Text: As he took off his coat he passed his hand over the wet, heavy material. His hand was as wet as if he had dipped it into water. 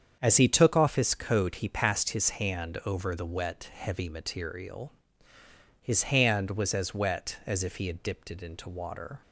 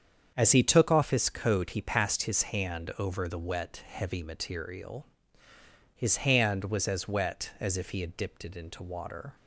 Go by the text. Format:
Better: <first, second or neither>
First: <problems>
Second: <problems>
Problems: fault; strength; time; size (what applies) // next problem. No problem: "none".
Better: neither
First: starts louder than the rest; strong; until 1.2 s; 7.5 dB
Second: starts louder than the rest; strong; until 1.3 s; 7.5 dB